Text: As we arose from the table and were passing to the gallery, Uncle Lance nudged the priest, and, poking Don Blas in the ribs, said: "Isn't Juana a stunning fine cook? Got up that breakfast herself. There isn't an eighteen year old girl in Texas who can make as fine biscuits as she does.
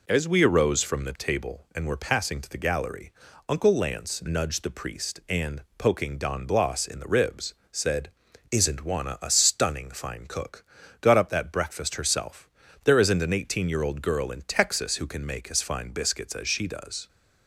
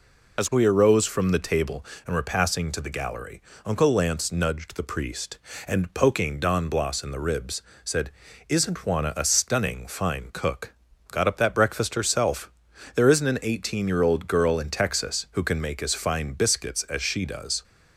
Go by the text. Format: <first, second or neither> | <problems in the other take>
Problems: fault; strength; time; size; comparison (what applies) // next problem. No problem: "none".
first | loses the start of "As"; at 0.3 s; 45 ms